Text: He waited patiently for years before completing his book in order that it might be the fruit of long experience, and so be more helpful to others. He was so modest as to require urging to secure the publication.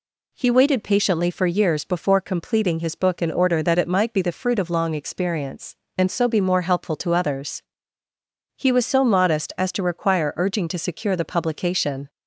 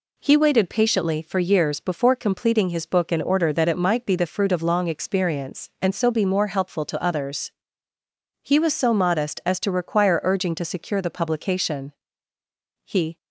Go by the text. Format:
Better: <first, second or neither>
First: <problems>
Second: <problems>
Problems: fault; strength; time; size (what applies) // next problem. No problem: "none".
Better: first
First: none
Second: goes on to say "He"; slight; from 12.8 s on; 0.32 s long